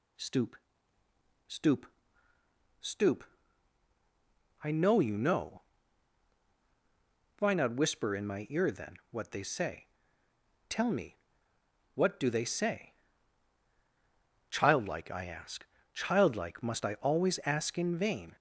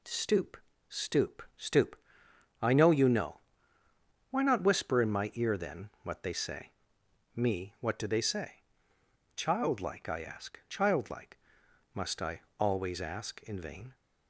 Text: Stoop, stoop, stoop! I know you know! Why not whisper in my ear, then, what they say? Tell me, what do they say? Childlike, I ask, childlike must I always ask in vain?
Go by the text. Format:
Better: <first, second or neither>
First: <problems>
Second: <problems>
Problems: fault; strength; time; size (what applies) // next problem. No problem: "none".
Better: first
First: none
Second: skips "Tell"; at 7.0 s // pauses between "childlike" and "must"; noticeable; at 11.3 s; 0.56 s long // pauses between "I" and "always"; slight; at 12.4 s; 0.18 s long